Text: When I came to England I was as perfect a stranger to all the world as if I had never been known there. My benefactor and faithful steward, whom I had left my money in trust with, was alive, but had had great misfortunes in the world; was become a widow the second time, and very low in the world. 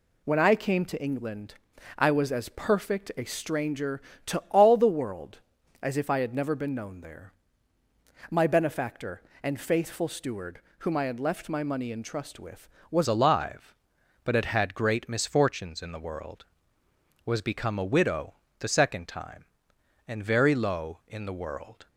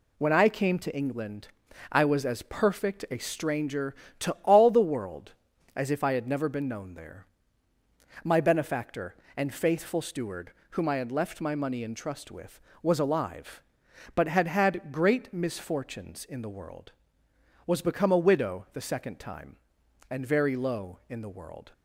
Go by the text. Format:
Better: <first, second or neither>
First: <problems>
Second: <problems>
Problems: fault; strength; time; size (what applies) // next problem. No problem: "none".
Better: second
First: pauses between "England" and "I"; at 1.5 s; 0.44 s long // changes voice at "alive"; from 13.0 s on; 8.8 s long // pauses between "widow" and "the"; slight; at 18.3 s; 0.22 s long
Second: pauses between "England" and "I"; at 1.4 s; 0.44 s long